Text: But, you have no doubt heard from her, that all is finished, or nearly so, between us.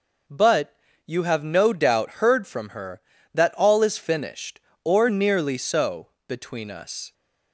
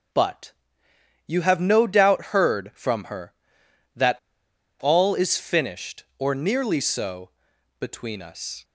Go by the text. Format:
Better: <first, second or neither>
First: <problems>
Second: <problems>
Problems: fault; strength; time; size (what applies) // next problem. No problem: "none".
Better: first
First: none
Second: starts louder than the rest; until 1.8 s; 6.5 dB // pauses between "that" and "all"; noticeable; at 4.1 s; 0.62 s long